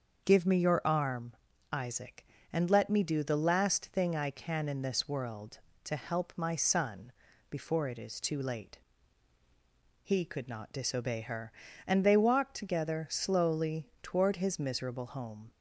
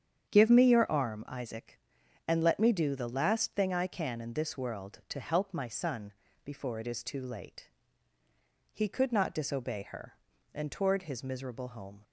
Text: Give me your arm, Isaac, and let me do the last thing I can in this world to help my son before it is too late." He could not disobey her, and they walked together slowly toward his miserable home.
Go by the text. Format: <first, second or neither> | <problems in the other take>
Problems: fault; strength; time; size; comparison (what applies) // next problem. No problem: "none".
first | starts louder than the rest; strong; until 1.3 s; 8.5 dB; also in the first // pauses between "son" and "before"; slight; at 6.1 s; 0.32 s long; also in the first // skips "they walked together slowly"; at 10.6 s